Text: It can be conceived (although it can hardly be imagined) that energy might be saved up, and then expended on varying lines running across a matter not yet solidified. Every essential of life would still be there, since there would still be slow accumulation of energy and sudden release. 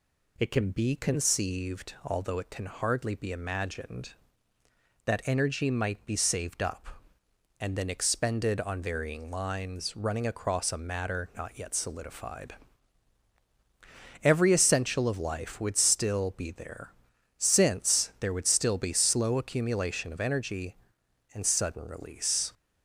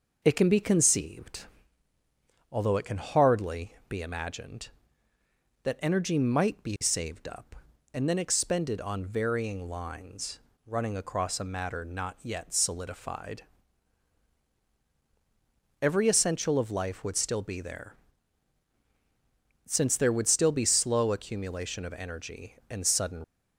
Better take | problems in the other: first | pauses between "lines" and "running"; slight; at 10.3 s; 0.26 s long // stops before "release"; at 23.2 s

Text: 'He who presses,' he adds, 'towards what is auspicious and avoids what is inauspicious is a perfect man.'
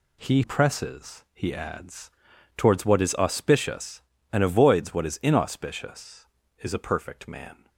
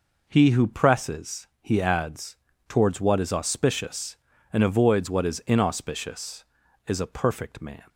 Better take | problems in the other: second | skips "who"; at 0.4 s

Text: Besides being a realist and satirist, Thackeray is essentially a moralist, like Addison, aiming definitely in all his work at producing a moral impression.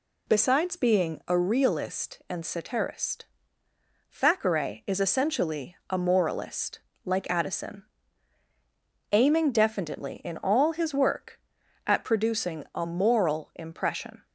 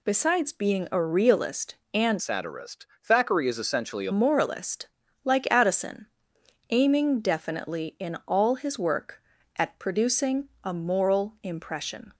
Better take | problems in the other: first | changes voice from "satirist" to "a"; from 2.1 to 4.1 s; 2.0 s long // pauses between "producing" and "a"; slight; at 10.4 s; 0.16 s long

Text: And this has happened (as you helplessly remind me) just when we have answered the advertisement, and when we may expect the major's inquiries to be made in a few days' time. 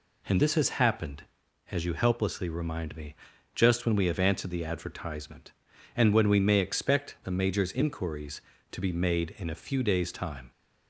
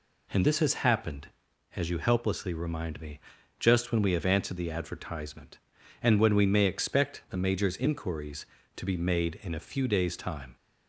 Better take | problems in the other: neither | none

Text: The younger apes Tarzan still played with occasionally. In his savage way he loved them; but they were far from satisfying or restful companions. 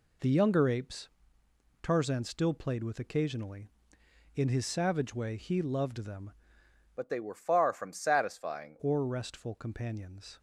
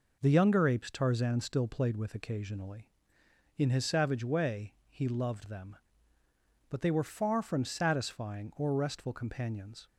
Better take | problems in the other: second | pauses between "apes" and "Tarzan"; noticeable; at 1.0 s; 0.74 s long // changes voice from "but" to "satisfying"; from 6.9 to 8.7 s; 1.8 s long

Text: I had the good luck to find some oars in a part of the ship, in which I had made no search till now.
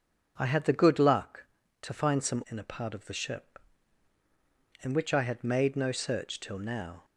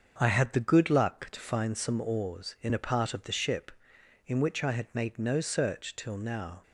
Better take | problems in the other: second | starts louder than the rest; until 1.3 s; 6.5 dB; also in the second // skips "oars"; at 2.4 s

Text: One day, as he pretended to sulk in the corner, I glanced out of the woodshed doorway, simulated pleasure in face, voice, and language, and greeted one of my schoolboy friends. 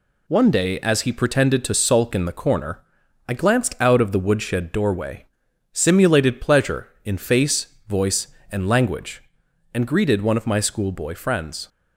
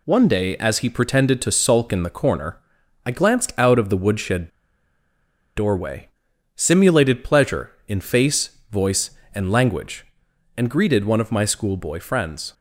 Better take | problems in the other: first | pauses between "woodshed" and "doorway"; at 4.4 s; 1.0 s long

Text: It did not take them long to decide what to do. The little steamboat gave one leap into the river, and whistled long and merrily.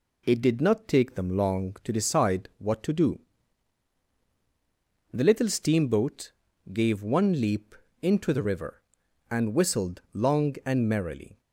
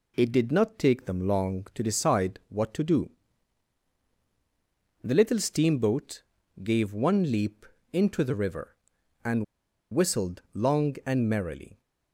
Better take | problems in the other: first | pauses between "steamboat" and "gave"; at 6.2 s; 0.40 s long; also in the first // pauses between "leap" and "into"; slight; at 7.6 s; 0.26 s long; slight in the first // pauses between "and" and "whistled"; noticeable; at 9.4 s; 0.49 s long

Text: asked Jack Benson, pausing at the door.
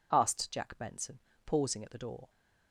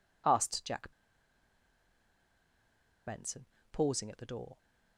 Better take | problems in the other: first | pauses between "Jack" and "Benson"; strong; at 0.9 s; 2.1 s long

